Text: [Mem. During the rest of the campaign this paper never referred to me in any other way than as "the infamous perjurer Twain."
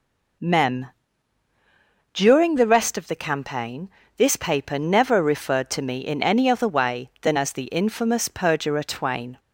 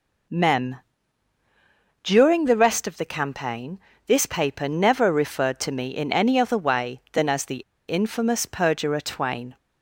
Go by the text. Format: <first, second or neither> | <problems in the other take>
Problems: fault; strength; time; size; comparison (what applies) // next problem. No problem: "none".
first | pauses between "campaign" and "this"; slight; at 3.7 s; 0.26 s long; slight in the first // pauses between "the" and "infamous"; slight; at 7.5 s; 0.32 s long